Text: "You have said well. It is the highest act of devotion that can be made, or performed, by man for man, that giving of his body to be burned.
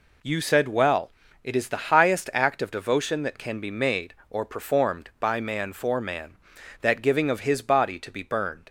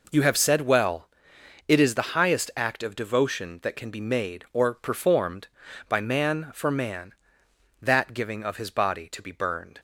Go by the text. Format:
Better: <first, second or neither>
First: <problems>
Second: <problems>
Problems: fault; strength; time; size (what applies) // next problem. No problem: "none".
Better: second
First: skips "have"; at 0.4 s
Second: none